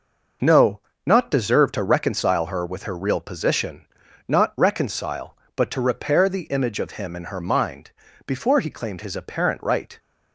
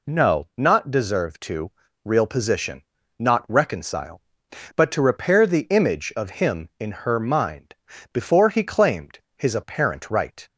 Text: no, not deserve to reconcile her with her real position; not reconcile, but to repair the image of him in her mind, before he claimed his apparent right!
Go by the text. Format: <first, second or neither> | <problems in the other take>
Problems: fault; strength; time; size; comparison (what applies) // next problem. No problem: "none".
first | skips "reconcile her with her"; at 1.8 s // pauses between "claimed" and "his"; slight; at 9.1 s; 0.18 s long